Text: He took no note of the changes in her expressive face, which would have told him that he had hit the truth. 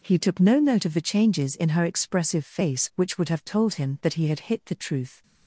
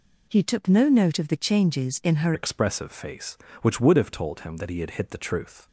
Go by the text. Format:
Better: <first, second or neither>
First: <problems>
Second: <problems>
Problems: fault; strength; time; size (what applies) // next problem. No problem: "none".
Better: first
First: none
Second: changes voice at "expressive"; from 2.3 s on; 3.3 s long